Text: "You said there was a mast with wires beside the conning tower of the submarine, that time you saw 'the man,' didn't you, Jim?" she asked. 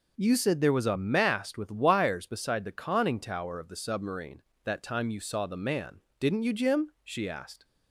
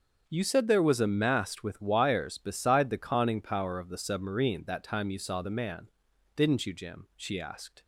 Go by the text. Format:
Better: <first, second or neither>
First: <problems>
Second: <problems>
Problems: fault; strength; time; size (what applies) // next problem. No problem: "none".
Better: first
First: none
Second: starts louder than the rest; until 1.2 s; 7 dB // says "power" for "tower"; at 3.4 s